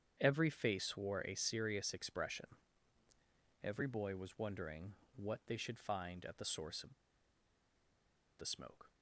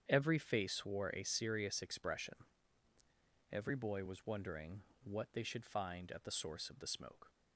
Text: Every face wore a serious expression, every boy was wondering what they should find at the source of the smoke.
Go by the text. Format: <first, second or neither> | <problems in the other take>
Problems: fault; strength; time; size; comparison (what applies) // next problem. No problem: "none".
second | starts louder than the rest; strong; until 1.2 s; 8 dB; strong in the second // pauses between "wondering" and "what"; slight; at 4.9 s; 0.22 s long; slight in the second // pauses between "of" and "the"; strong; at 6.9 s; 1.4 s long